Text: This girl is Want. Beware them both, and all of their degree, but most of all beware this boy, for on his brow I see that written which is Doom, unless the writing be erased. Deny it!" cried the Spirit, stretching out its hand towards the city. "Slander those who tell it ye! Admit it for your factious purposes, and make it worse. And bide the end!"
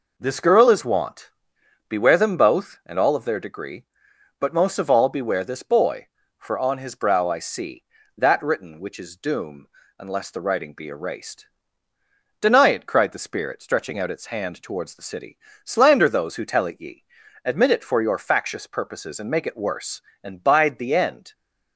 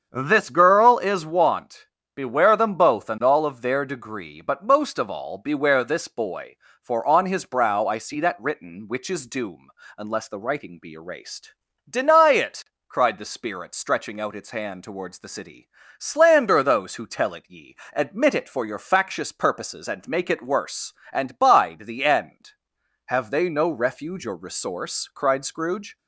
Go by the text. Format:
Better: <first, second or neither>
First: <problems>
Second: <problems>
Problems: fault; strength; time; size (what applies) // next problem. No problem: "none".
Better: first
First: none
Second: starts louder than the rest; strong; until 1.1 s; 8 dB // goes on to say "Have they no refuge or resource cried Scrooge"; strong; from 23.0 s on; 2.9 s long